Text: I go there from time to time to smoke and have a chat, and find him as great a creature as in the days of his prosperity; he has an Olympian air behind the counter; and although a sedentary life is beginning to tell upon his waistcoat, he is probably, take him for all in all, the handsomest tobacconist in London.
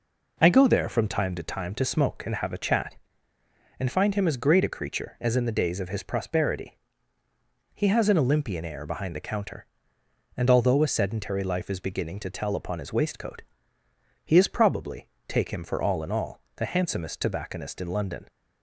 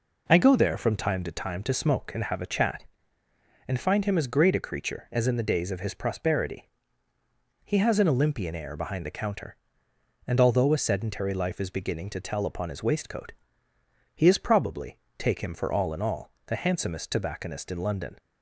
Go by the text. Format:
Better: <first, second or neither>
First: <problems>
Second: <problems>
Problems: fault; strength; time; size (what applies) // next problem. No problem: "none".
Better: neither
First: none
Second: none